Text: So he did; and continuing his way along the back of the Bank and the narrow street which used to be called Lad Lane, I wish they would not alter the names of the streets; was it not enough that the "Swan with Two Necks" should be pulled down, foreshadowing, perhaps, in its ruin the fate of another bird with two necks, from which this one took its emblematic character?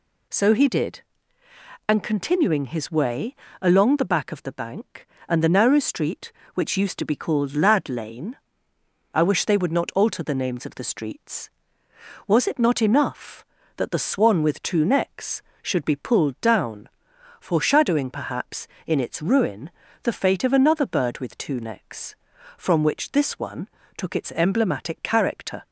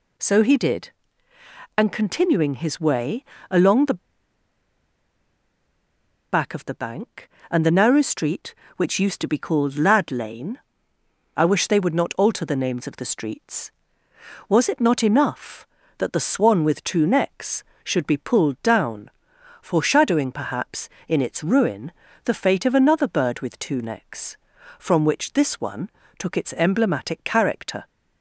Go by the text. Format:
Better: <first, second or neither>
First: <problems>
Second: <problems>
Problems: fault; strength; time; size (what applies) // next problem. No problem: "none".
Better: first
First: pauses between "way" and "along"; slight; at 3.3 s; 0.28 s long // pauses between "ruin" and "the"; slight; at 19.7 s; 0.32 s long // pauses between "one" and "took"; slight; at 23.6 s; 0.30 s long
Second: pauses between "way" and "along"; slight; at 3.2 s; 0.28 s long // pauses between "the" and "back"; strong; at 3.9 s; 2.3 s long // pauses between "ruin" and "the"; slight; at 21.9 s; 0.32 s long // pauses between "one" and "took"; slight; at 25.8 s; 0.30 s long